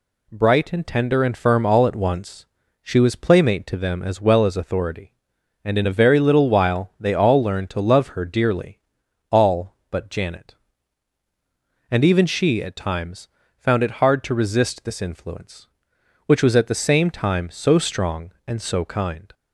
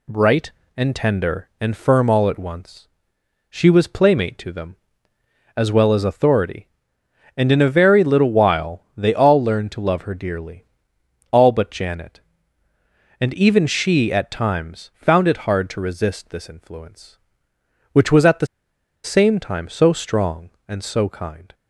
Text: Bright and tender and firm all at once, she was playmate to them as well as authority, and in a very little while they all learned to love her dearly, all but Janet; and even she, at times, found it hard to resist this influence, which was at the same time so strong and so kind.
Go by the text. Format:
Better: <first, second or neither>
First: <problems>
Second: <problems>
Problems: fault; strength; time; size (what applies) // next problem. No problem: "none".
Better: first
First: none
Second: pauses between "the" and "same"; noticeable; at 18.4 s; 0.57 s long